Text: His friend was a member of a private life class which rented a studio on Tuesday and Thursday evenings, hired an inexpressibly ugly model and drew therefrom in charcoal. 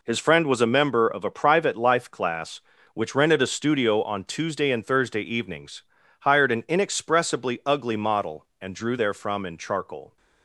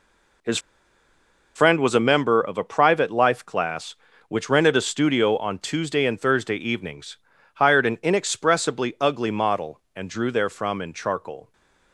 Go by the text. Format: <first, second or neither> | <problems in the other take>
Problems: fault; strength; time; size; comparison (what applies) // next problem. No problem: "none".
first | pauses between "His" and "friend"; noticeable; at 0.5 s; 0.97 s long